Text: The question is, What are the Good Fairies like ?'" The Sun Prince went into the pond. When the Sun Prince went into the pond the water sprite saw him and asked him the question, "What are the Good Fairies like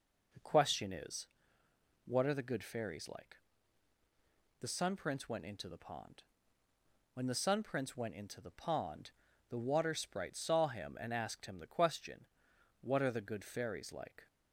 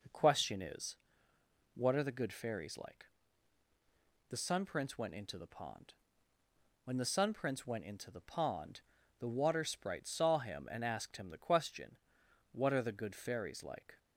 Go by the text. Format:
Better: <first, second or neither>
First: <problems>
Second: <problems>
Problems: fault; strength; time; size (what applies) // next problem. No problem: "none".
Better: neither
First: pauses between "pond" and "the"; slight; at 9.1 s; 0.36 s long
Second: pauses between "pond" and "the"; slight; at 8.8 s; 0.36 s long